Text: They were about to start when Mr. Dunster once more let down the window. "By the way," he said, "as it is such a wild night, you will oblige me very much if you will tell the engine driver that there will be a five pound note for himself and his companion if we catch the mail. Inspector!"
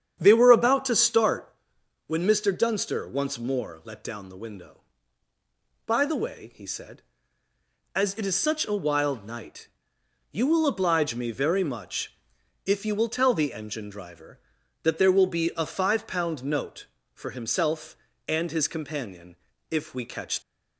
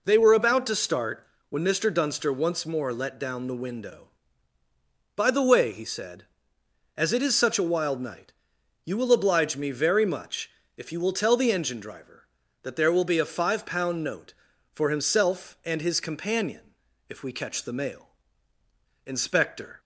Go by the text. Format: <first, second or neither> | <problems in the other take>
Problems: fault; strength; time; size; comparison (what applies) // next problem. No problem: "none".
second | starts louder than the rest; strong; until 1.2 s; 8.5 dB // pauses between "start" and "when"; noticeable; at 1.5 s; 0.54 s long; slight in the second // pauses between "much" and "if"; noticeable; at 12.1 s; 0.48 s long; slight in the second // pauses between "companion" and "if"; slight; at 19.3 s; 0.34 s long; slight in the second // stops before "the mail Inspector"; at 20.4 s